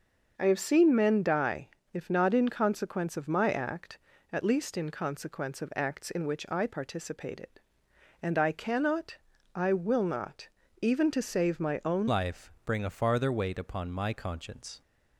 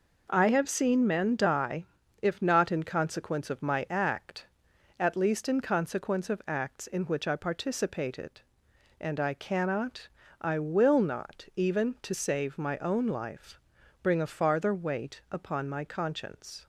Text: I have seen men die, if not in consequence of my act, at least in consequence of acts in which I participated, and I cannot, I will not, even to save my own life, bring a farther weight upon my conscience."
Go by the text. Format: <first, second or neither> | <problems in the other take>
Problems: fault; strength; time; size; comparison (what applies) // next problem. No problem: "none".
second | starts louder than the rest; noticeable; until 1.3 s; 6 dB // changes voice at "life"; from 12.0 s on; 2.8 s long